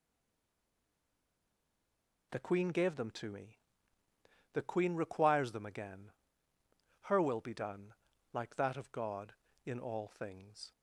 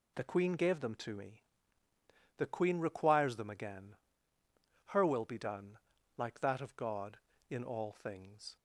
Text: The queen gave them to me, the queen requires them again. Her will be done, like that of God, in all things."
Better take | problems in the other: second | stays silent before the first word; until 2.3 s; 2.3 s long

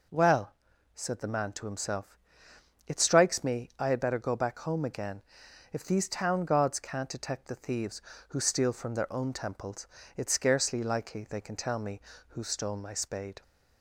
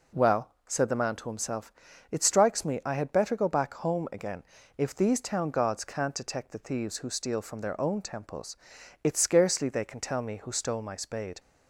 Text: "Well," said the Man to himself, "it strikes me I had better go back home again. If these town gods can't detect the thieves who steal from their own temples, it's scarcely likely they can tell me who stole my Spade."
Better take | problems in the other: first | skips "likely"; at 9.6 s

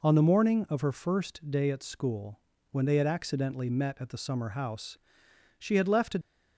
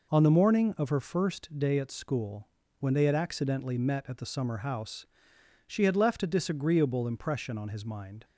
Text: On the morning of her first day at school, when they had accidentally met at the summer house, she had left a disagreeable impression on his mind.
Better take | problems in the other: second | stops before "disagreeable impression on his mind"; at 6.2 s

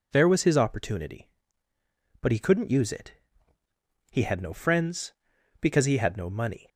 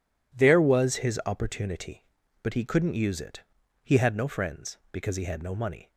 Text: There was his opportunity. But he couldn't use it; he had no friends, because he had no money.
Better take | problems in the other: neither | none

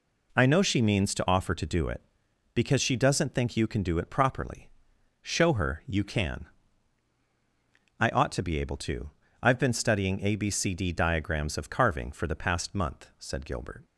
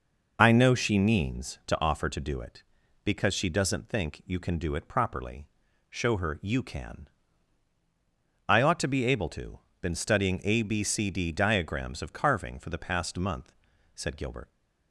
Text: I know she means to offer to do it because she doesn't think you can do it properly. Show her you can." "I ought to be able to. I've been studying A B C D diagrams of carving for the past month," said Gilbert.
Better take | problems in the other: first | skips "I've"; at 9.7 s

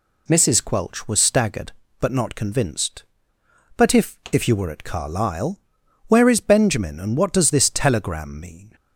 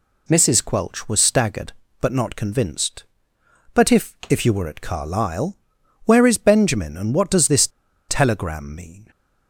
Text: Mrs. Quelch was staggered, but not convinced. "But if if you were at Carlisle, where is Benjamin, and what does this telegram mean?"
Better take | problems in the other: first | pauses between "this" and "telegram"; at 7.6 s; 0.40 s long

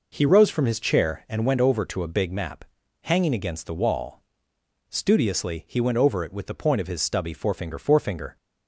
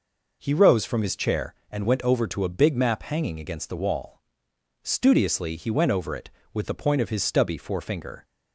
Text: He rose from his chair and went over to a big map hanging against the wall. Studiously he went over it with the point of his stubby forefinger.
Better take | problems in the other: second | pauses between "map" and "hanging"; at 2.6 s; 0.40 s long // says "forefinger" twice; at 7.7 s

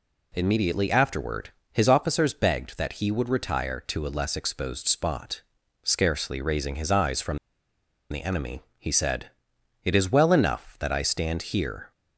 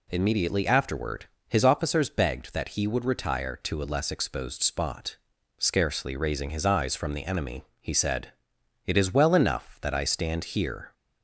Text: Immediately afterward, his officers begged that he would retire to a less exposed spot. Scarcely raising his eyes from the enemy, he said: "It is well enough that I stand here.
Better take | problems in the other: second | pauses between "from" and "the"; noticeable; at 7.3 s; 0.73 s long

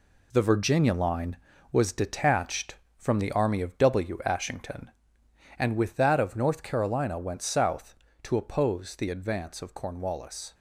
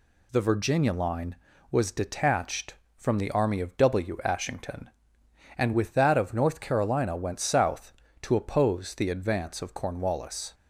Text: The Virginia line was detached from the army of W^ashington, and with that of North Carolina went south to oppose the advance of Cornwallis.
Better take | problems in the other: second | gets quieter; strong; throughout; 8 dB

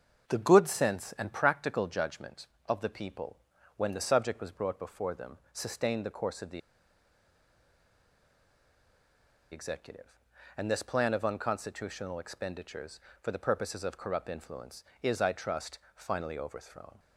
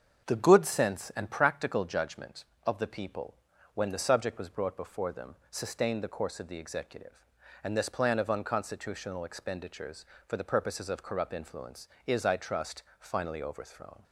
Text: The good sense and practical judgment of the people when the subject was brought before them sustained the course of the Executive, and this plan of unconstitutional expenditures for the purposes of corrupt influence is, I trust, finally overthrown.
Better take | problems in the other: second | starts louder than the rest; until 1.3 s; 7 dB; also in the second // pauses between "people" and "when"; at 3.3 s; 0.40 s long; also in the second // pauses between "the" and "Executive"; strong; at 6.6 s; 2.9 s long

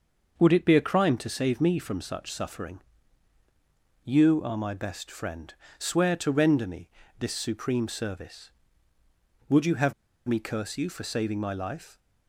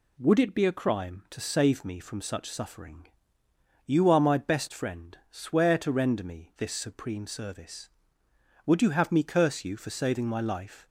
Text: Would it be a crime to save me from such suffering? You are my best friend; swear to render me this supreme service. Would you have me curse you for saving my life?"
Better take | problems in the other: second | starts louder than the rest; until 1.4 s; 6 dB // pauses between "me" and "this"; slight; at 6.8 s; 0.28 s long // pauses between "have" and "me"; slight; at 9.9 s; 0.35 s long

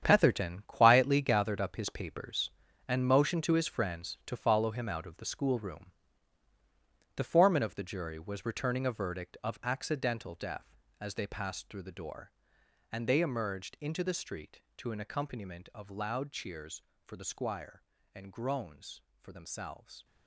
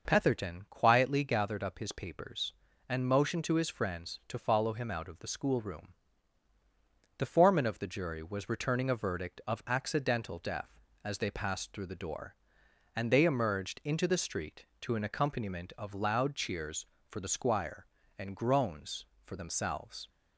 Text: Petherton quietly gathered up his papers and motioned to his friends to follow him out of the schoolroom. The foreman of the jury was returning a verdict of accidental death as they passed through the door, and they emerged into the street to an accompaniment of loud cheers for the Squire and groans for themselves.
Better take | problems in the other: second | gets quieter; strong; throughout; 11.5 dB

